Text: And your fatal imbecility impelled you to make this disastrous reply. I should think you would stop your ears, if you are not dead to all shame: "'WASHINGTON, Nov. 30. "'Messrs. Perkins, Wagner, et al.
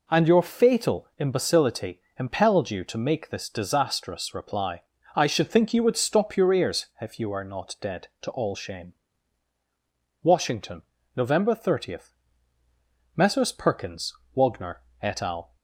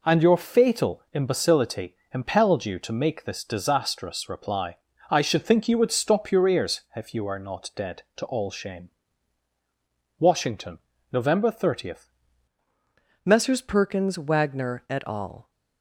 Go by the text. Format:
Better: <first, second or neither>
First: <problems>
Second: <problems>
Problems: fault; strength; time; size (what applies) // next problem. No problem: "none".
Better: first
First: pauses between "imbecility" and "impelled"; slight; at 1.9 s; 0.20 s long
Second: pauses between "imbecility" and "impelled"; slight; at 1.9 s; 0.20 s long // changes voice at "Messrs"; from 13.2 s on; 2.3 s long